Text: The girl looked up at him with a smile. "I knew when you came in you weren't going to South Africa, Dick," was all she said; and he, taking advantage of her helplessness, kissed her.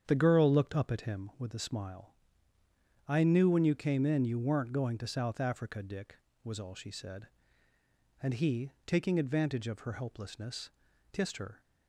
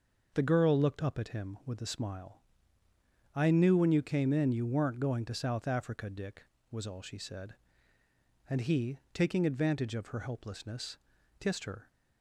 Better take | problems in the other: second | starts louder than the rest; strong; until 1.2 s; 8 dB

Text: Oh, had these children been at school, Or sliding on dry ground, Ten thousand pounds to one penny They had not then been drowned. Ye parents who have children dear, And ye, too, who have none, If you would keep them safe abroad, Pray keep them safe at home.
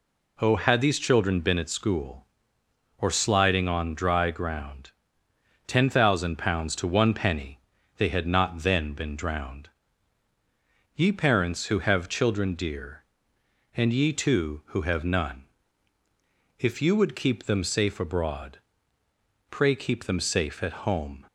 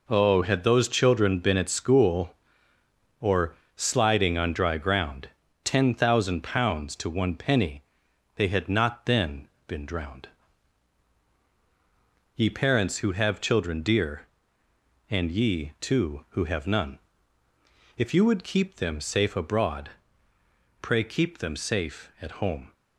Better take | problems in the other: first | says "those" for "these"; at 0.6 s // pauses between "Or" and "sliding"; slight; at 3.5 s; 0.20 s long // pauses between "penny" and "They"; noticeable; at 7.8 s; 0.52 s long; also in the first // pauses between "then" and "been"; slight; at 9.4 s; 0.20 s long

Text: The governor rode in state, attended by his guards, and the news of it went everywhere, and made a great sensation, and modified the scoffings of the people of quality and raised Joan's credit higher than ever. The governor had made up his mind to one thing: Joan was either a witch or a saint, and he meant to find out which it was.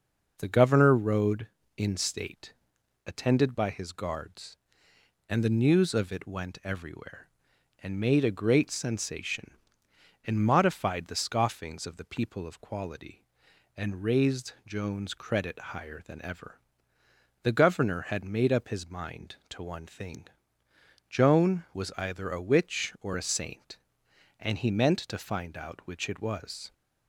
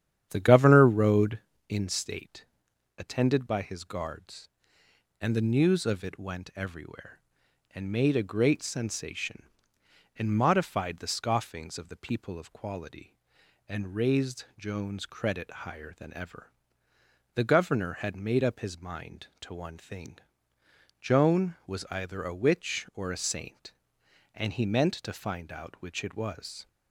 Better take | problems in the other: first | starts louder than the rest; strong; until 1.6 s; 10 dB

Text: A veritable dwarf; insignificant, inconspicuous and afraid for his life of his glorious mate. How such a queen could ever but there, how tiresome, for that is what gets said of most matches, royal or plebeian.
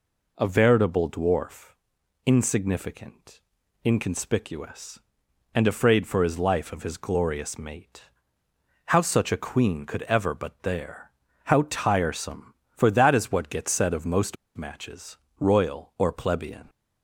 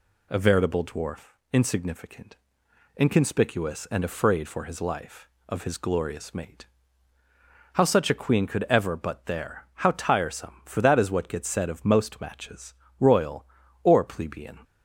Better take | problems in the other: second | pauses between "most" and "matches"; slight; at 14.3 s; 0.20 s long

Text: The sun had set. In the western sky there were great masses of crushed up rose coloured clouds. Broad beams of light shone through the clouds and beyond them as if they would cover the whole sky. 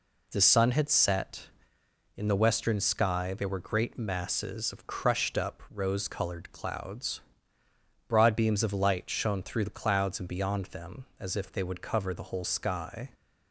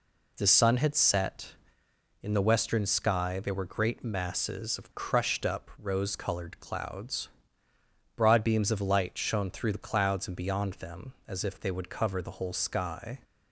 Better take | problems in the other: neither | none

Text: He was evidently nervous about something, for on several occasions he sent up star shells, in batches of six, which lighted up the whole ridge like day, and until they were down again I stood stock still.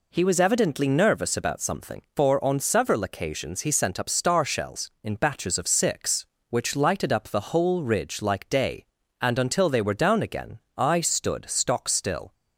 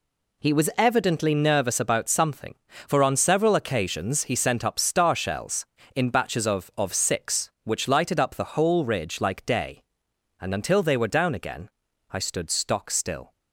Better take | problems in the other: first | says "of" twice; at 6.7 s // pauses between "again" and "I"; at 11.6 s; 0.42 s long; slight in the first

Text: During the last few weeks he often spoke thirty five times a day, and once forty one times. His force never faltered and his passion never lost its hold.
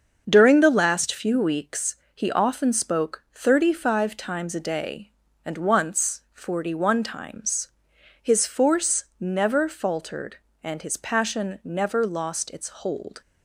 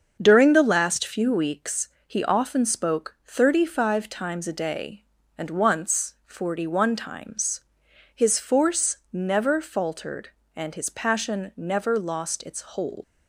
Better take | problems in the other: first | starts louder than the rest; until 1.2 s; 6.5 dB; also in the first // pauses between "weeks" and "he"; slight; at 1.8 s; 0.18 s long; slight in the first // leaves "hold" unfinished; at 13.0 s; 95 ms

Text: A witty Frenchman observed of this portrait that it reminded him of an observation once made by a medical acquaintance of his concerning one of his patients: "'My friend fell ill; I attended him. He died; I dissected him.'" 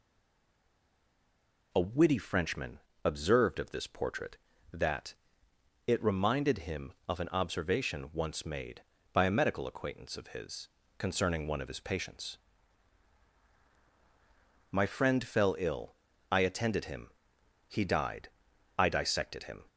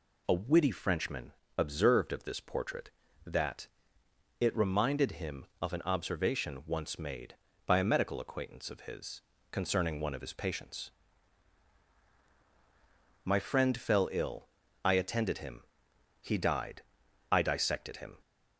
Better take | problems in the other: second | stays silent before the first word; noticeable; until 1.7 s; 1.7 s long // pauses between "Frenchman" and "observed"; slight; at 2.7 s; 0.26 s long; slight in the second // pauses between "that" and "it"; noticeable; at 5.1 s; 0.74 s long; noticeable in the second // pauses between "his" and "concerning"; slight; at 10.6 s; 0.30 s long; slight in the second

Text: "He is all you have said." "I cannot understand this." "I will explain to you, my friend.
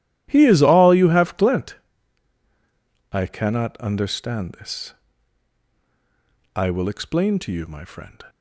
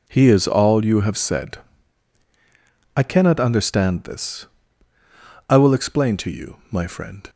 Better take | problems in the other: second | says "glent" for "said"; at 1.3 s

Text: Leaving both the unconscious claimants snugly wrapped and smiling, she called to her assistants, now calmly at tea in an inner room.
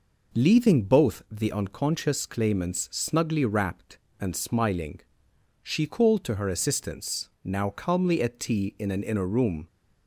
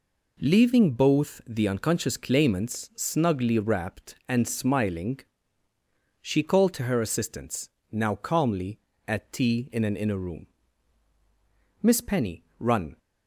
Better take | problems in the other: first | goes on to say "Miss Penny run"; noticeable; from 11.8 s on; 1.1 s long

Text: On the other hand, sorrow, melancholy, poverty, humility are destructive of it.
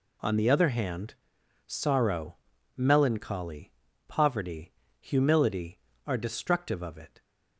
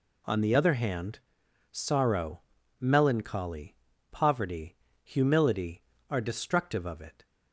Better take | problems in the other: neither | none

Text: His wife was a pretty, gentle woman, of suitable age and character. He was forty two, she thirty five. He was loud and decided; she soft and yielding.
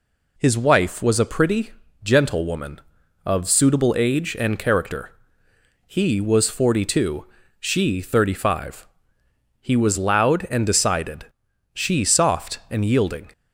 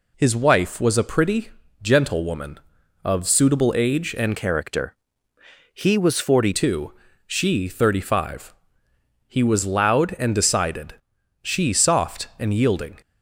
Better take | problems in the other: first | changes voice from "character" to "forty"; from 4.3 to 6.5 s; 2.2 s long

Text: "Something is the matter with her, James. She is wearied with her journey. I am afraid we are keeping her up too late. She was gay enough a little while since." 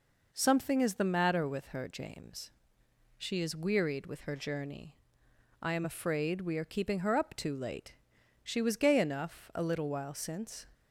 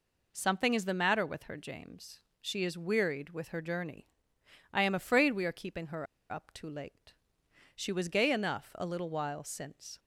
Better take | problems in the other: first | pauses between "her" and "up"; slight; at 6.0 s; 0.24 s long

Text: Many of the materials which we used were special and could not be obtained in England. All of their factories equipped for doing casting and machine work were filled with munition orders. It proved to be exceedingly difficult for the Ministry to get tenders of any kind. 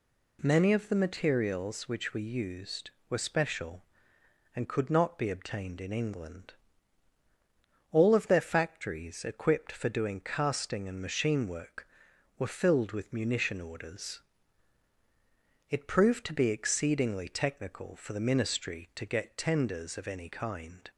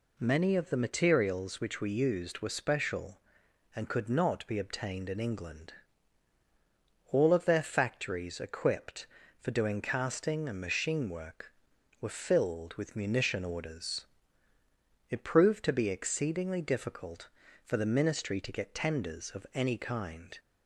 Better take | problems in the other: second | says "technical" for "difficult"; at 17.2 s

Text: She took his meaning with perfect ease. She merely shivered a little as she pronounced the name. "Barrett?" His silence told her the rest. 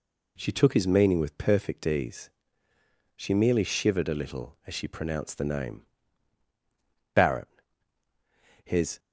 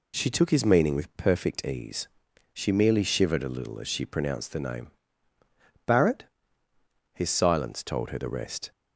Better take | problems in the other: second | stops before "silence told her the rest"; at 8.9 s

